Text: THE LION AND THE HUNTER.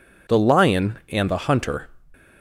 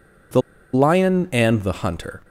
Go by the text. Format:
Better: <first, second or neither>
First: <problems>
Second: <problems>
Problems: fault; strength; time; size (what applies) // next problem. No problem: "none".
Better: first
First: none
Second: pauses between "THE" and "LION"; slight; at 0.4 s; 0.33 s long